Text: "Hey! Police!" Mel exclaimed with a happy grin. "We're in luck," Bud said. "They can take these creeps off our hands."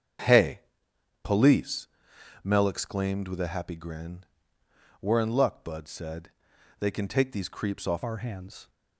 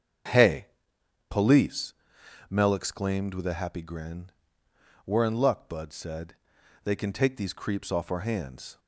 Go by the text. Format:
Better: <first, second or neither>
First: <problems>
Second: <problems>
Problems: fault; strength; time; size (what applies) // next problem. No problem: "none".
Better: second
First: starts louder than the rest; strong; until 1.8 s; 8 dB // changes voice at "our"; from 8.0 s on; 0.6 s long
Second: starts louder than the rest; strong; until 1.9 s; 8 dB